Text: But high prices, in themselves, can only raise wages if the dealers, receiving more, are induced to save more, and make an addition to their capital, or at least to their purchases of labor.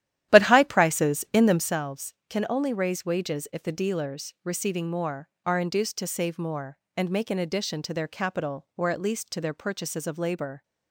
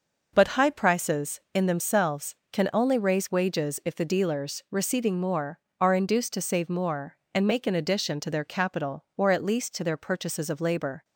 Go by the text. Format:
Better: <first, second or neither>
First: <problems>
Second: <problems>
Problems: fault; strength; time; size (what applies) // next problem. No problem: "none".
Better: second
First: starts louder than the rest; strong; until 1.8 s; 12 dB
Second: none